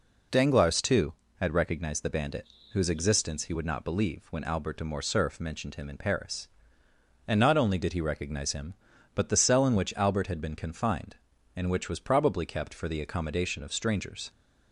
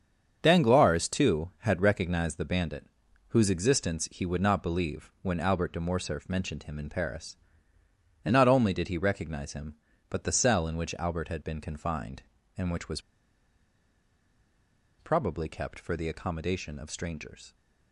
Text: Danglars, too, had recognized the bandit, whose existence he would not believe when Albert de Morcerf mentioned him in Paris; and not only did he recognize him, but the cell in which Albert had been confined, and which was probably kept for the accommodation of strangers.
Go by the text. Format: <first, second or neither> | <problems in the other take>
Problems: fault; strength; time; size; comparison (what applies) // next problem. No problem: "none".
first | starts louder than the rest; strong; until 1.4 s; 7 dB // pauses between "was" and "probably"; strong; at 13.0 s; 1.9 s long